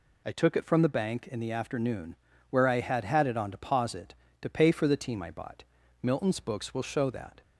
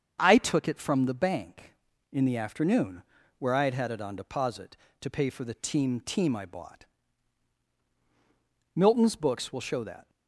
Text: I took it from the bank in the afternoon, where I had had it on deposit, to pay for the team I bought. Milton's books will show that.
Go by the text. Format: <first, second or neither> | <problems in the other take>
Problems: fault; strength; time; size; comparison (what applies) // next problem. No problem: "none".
first | starts louder than the rest; until 1.2 s; 7 dB // says "team" twice; at 6.0 s